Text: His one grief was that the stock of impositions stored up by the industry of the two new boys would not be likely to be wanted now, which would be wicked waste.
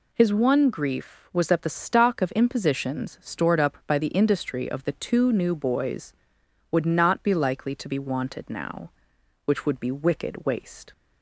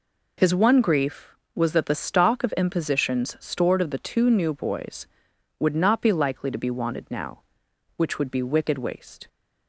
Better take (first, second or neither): first